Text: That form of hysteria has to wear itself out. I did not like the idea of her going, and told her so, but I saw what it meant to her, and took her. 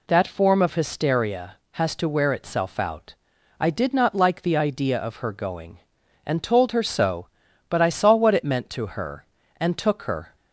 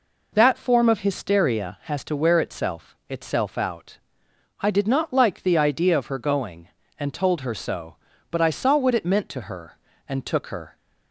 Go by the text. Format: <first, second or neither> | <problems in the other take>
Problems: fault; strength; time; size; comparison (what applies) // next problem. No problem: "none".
first | says "itself" twice; at 3.0 s